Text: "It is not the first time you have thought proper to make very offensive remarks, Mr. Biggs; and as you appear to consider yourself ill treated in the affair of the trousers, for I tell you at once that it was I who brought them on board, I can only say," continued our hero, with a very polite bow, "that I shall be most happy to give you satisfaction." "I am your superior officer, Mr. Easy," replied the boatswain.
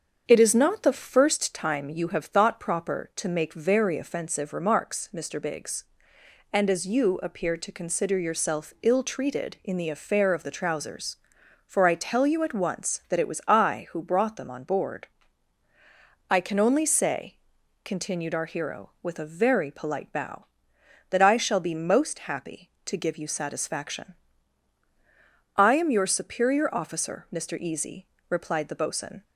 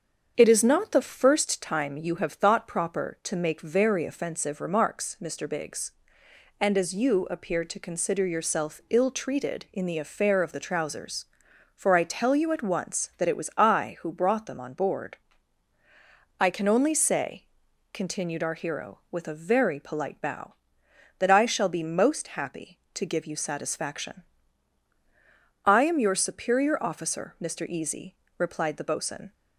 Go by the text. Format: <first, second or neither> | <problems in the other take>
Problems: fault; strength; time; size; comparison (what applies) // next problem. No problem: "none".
neither | starts louder than the rest; strong; the same in both